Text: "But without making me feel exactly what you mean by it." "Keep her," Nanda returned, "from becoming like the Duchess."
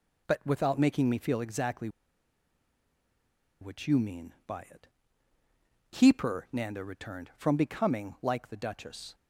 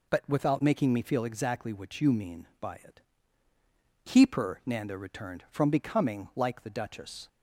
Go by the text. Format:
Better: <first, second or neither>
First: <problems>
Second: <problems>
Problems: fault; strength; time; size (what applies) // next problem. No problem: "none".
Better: second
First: pauses between "exactly" and "what"; strong; at 1.8 s; 1.7 s long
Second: none